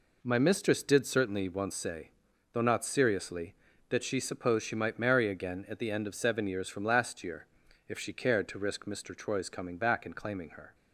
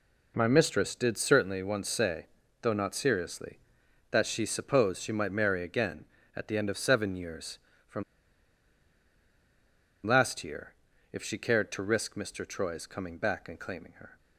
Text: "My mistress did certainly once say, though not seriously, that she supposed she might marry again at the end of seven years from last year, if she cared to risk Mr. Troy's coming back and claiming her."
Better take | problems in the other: first | pauses between "from" and "last"; strong; at 8.0 s; 2.0 s long

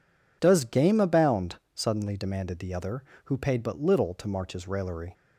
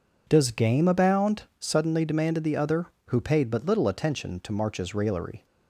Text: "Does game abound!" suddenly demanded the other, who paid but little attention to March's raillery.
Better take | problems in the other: second | skips "attention"; at 4.1 s

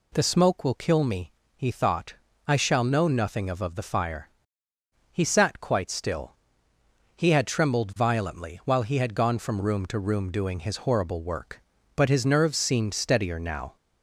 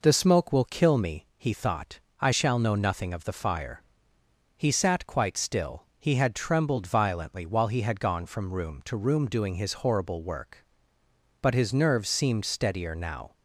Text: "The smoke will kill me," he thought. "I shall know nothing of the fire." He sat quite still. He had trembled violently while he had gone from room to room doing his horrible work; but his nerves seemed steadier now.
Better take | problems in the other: second | says "of" twice; at 3.6 s

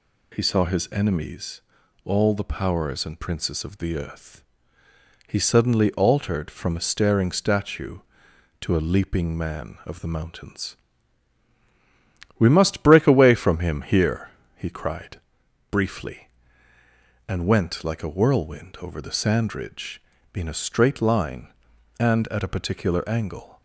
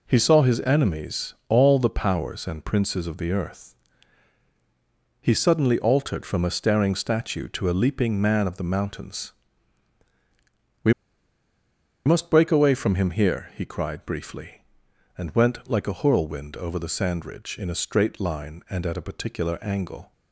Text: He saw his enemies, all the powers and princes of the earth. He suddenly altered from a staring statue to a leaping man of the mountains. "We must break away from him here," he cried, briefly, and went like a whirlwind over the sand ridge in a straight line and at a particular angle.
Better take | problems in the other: first | pauses between "We" and "must"; at 10.9 s; 1.1 s long

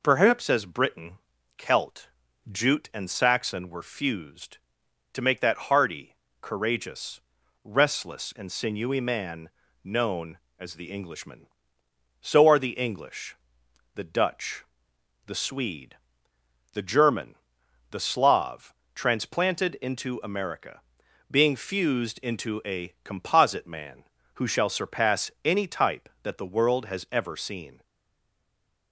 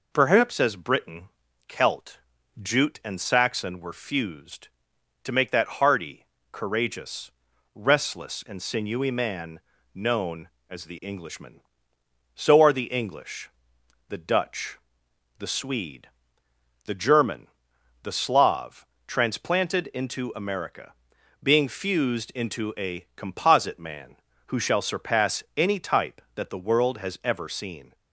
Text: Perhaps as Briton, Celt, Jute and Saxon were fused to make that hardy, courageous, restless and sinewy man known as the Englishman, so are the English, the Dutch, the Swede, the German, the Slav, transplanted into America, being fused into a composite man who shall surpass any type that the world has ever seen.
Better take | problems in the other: second | pauses between "man" and "known"; slight; at 9.4 s; 0.34 s long; slight in the second // stays silent after the last word; from 27.8 s on; 1.1 s long

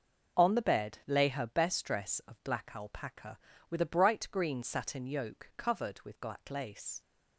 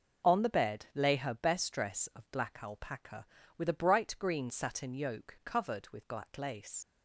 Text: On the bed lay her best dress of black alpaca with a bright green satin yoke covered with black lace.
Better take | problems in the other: first | leaves "lace" unfinished; at 6.8 s; 60 ms

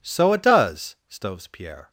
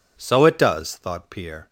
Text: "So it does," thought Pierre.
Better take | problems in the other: second | says "stoves" for "thought"; at 1.0 s

